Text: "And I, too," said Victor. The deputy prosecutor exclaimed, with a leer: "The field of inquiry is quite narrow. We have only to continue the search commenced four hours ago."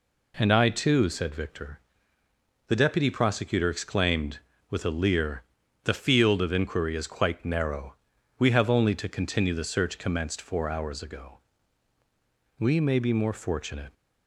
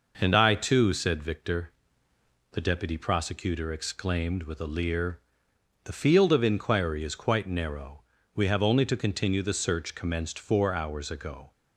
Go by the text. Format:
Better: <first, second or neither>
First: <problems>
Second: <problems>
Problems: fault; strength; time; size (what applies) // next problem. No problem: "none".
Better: second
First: goes on to say "We may be more fortunate"; from 12.5 s on; 1.3 s long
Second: none